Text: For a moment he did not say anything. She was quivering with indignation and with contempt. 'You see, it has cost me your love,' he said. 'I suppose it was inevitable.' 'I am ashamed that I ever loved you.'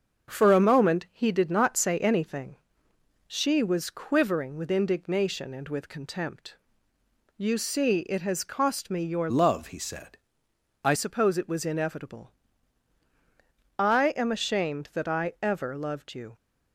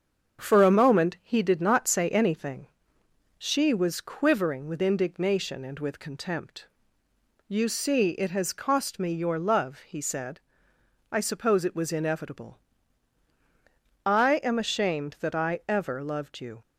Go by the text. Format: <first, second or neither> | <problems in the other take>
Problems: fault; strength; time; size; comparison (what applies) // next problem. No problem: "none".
second | starts louder than the rest; until 1.3 s; 6.5 dB; also in the second // changes voice from "love" to "I"; from 9.3 to 10.9 s; 1.6 s long